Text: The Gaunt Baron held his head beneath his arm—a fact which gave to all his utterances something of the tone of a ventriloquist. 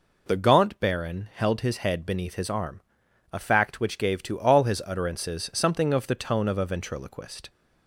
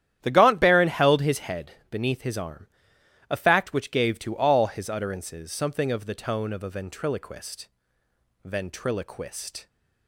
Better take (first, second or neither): first